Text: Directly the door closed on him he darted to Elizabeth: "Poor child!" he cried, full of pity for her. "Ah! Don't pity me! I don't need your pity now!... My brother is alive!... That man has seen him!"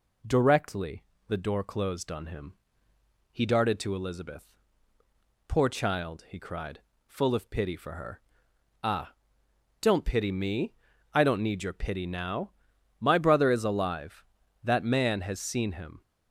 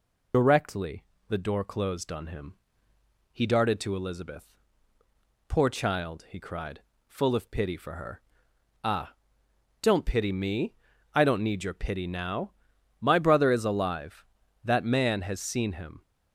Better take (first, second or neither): first